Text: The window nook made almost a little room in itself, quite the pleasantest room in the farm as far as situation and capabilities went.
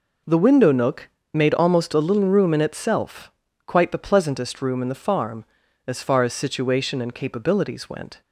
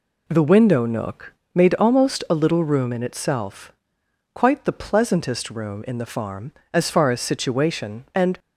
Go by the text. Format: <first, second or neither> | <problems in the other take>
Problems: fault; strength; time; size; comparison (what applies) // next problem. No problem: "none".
first | pauses between "nook" and "made"; slight; at 1.3 s; 0.22 s long; slight in the first // stops before "capabilities went"; at 8.3 s